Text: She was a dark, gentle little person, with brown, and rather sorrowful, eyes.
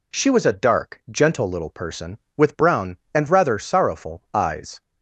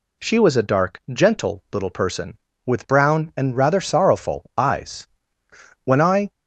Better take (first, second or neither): first